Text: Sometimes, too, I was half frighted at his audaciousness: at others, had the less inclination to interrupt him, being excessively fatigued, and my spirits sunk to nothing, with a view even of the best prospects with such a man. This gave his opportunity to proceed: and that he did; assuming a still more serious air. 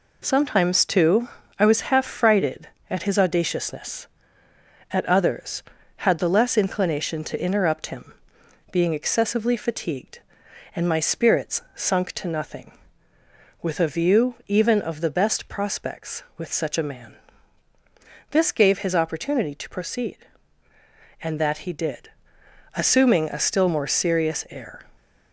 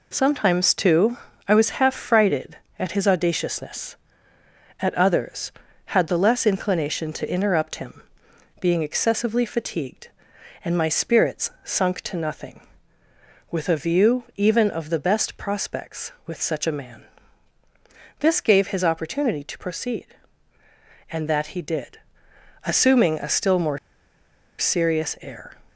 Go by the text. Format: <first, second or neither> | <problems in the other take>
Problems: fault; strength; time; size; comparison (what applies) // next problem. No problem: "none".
first | pauses between "more" and "serious"; noticeable; at 23.7 s; 0.80 s long